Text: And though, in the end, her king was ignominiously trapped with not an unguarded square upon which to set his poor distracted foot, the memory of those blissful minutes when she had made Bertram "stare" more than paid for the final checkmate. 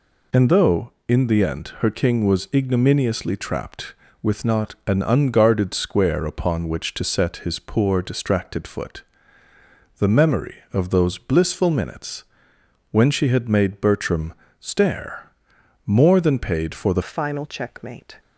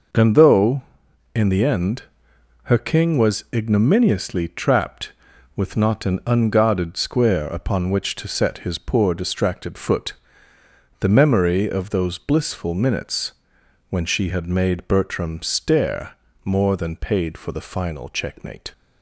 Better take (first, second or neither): second